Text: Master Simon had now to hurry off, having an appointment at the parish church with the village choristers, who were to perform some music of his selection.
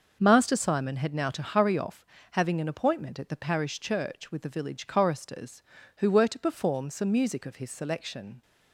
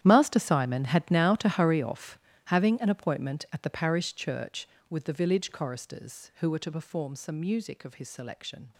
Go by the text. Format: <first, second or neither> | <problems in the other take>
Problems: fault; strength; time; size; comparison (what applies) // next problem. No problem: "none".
first | gets quieter; strong; throughout; 16.5 dB // starts louder than the rest; strong; until 1.0 s; 11 dB; noticeable in the first